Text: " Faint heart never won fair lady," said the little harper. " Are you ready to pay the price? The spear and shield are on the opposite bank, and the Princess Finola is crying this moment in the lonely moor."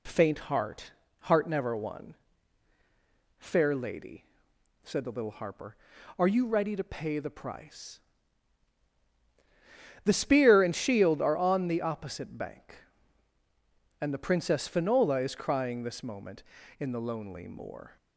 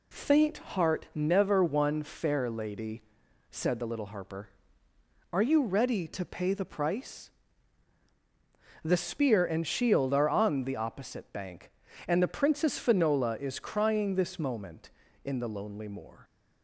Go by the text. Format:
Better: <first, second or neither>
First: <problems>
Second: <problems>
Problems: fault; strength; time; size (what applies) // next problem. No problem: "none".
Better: second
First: says "heart" twice; at 1.2 s // pauses between "won" and "fair"; strong; at 2.1 s; 1.2 s long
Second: none